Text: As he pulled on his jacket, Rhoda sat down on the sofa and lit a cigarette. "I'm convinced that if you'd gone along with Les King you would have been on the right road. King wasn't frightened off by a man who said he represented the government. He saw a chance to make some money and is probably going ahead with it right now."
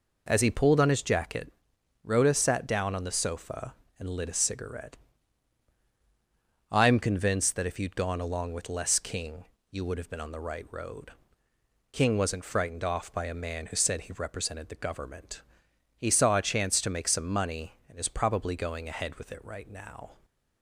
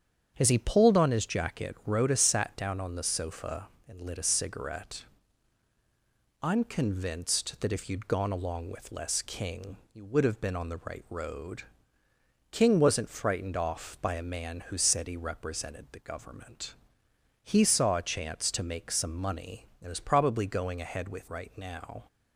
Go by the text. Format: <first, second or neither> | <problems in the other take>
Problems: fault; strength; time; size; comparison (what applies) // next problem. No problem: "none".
first | starts louder than the rest; strong; until 1.3 s; 8 dB // pauses between "King" and "you"; slight; at 9.7 s; 0.16 s long; slight in the first // skips "it"; at 21.2 s